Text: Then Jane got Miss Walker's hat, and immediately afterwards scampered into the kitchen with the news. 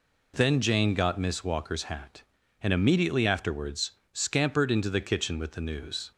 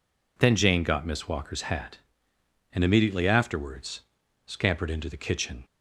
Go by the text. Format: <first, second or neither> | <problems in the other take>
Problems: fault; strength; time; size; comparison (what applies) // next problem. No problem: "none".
first | pauses between "afterwards" and "scampered"; noticeable; at 4.0 s; 0.48 s long; slight in the first // stops before "with the news"; at 5.6 s